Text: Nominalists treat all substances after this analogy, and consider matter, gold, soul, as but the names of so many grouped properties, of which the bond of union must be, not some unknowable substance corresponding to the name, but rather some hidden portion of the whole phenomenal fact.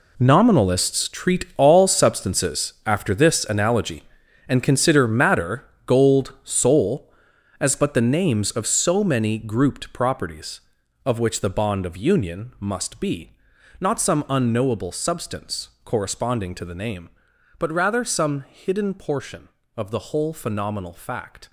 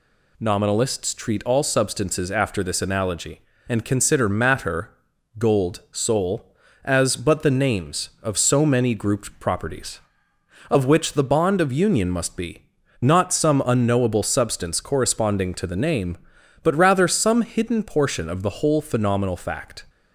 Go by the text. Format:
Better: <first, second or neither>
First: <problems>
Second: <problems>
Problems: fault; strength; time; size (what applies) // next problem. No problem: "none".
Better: second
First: gets quieter; strong; throughout; 13.5 dB // pauses between "substance" and "corresponding"; slight; at 15.6 s; 0.16 s long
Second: none